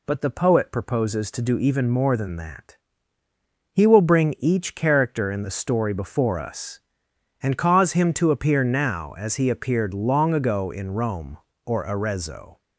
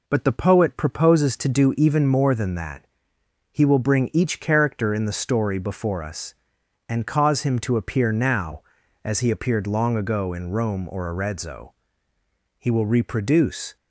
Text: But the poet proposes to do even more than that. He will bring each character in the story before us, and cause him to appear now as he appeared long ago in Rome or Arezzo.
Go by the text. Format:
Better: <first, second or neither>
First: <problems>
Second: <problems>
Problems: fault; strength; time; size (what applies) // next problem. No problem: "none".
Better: first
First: none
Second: goes on to say "He will reproduce"; noticeable; from 12.5 s on; 1.1 s long